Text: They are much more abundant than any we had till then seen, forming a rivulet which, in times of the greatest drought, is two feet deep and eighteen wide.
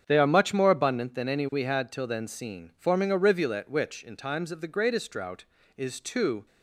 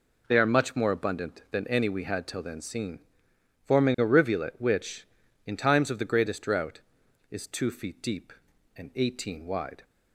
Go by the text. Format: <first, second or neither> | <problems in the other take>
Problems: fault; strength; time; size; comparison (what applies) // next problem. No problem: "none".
second | starts louder than the rest; strong; until 1.0 s; 7.5 dB // stops before "feet deep and eighteen wide"; at 6.4 s